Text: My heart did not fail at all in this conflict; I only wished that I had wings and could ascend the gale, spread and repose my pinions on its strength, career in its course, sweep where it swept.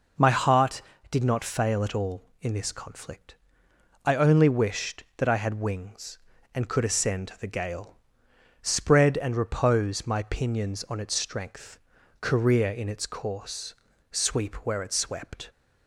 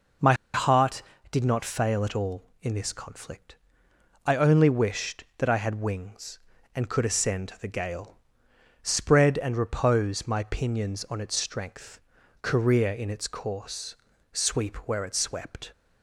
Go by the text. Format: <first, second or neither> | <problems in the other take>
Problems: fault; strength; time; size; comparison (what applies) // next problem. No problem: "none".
first | pauses between "My" and "heart"; slight; at 0.3 s; 0.19 s long